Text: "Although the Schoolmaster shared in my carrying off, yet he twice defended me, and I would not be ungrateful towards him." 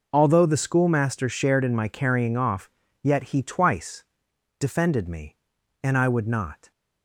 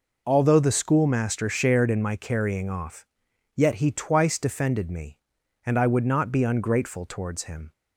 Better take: second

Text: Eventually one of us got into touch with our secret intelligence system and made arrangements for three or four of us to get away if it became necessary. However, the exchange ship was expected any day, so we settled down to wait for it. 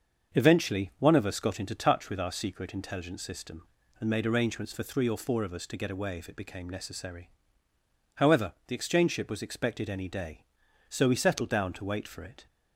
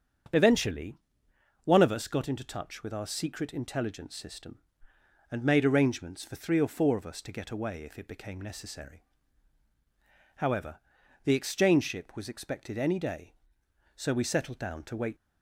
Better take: first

